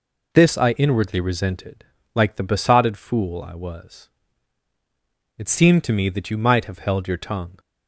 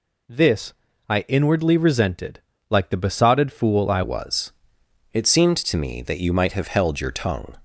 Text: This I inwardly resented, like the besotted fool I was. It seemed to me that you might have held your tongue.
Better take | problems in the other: first | pauses between "This" and "I"; slight; at 0.7 s; 0.34 s long // changes voice at "was"; from 4.0 s on; 3.5 s long

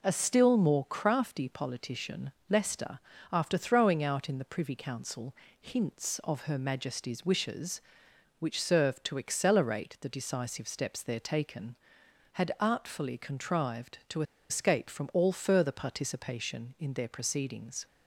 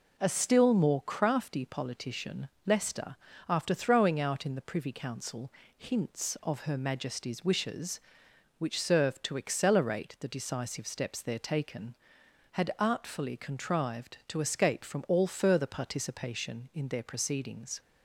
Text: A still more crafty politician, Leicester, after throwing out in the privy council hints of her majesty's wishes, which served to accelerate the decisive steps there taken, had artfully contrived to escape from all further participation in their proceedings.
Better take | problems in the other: second | pauses between "council" and "hints"; slight; at 5.3 s; 0.26 s long; slight in the second // pauses between "to" and "escape"; slight; at 14.2 s; 0.27 s long

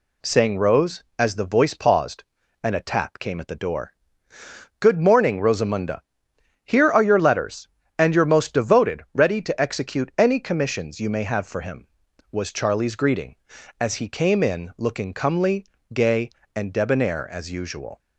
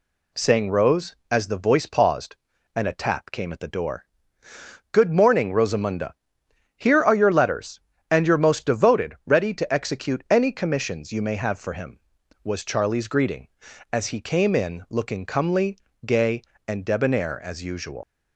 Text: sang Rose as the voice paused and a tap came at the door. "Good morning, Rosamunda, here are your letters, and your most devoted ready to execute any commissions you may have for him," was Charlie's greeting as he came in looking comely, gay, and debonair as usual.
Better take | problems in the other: first | leaves "usual" unfinished; at 18.0 s; 75 ms

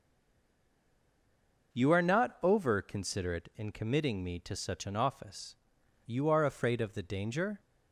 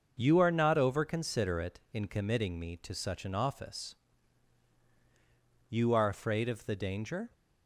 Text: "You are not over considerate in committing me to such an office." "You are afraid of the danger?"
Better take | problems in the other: second | stays silent before the first word; noticeable; until 1.7 s; 1.7 s long

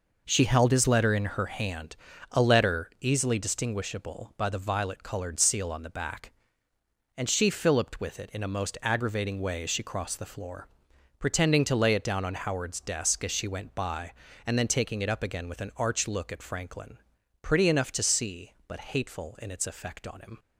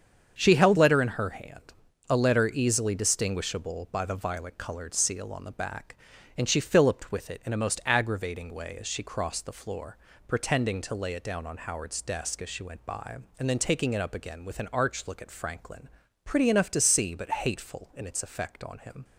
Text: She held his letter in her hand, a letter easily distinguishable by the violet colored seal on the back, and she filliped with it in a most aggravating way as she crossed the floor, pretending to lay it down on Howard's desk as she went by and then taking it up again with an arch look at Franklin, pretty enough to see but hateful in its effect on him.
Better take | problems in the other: first | starts louder than the rest; strong; until 1.4 s; 7.5 dB // skips "his"; at 0.7 s

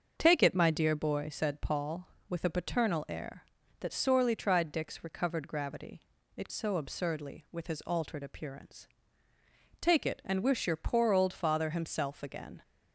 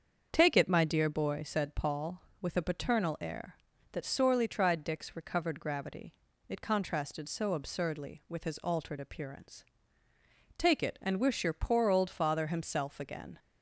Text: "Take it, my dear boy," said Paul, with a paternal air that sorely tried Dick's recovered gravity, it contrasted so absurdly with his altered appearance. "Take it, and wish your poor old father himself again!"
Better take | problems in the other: second | starts louder than the rest; until 1.1 s; 6.5 dB; also in the second // skips "contrasted"; at 6.4 s

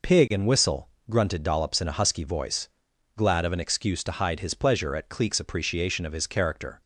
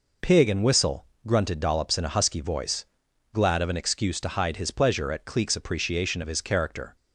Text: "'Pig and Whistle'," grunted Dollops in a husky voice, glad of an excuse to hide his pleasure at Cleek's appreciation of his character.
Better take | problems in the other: neither | none

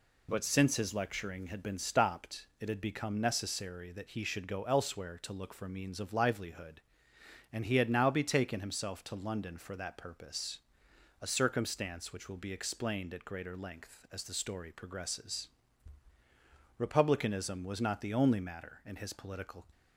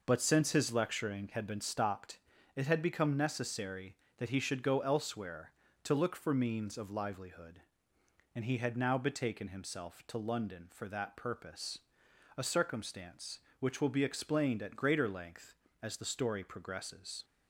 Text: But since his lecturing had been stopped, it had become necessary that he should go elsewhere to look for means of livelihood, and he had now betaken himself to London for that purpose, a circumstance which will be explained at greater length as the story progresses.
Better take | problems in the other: second | goes on to say "Republicanism was not the only matter in his political"; strong; from 16.7 s on; 2.8 s long

